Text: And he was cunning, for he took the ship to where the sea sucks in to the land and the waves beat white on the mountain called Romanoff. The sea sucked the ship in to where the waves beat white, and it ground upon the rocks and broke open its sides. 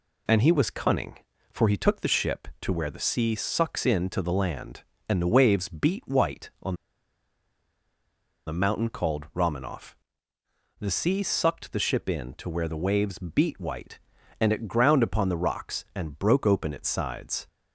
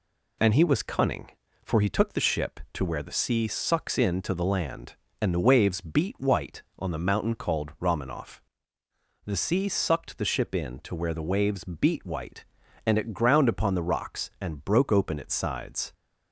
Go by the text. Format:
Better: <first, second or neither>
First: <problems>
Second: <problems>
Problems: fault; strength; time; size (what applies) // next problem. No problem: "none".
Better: second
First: pauses between "on" and "the"; strong; at 6.7 s; 1.7 s long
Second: none